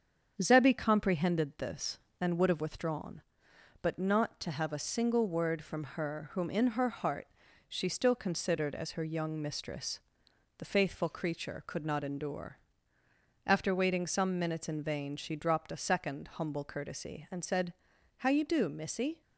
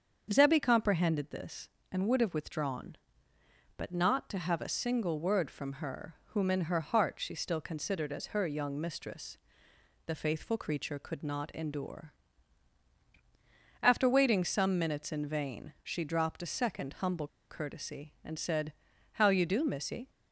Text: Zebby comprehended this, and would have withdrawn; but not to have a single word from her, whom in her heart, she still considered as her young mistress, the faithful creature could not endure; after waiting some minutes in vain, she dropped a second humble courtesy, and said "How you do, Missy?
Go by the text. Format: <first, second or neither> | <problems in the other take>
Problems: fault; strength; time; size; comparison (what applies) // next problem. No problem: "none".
first | starts louder than the rest; until 1.3 s; 7 dB; strong in the first // pauses between "humble" and "courtesy"; slight; at 17.2 s; 0.22 s long // pauses between "said" and "How"; at 18.7 s; 0.38 s long; noticeable in the first